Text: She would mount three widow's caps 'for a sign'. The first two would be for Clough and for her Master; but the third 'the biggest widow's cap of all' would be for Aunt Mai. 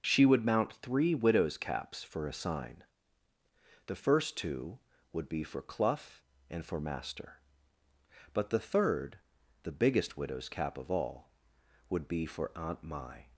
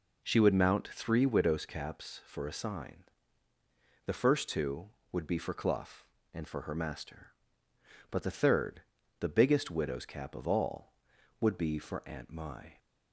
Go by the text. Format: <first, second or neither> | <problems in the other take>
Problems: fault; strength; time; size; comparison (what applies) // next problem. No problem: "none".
second | skips "her"; at 6.7 s // pauses between "third" and "the"; noticeable; at 9.1 s; 0.46 s long; slight in the second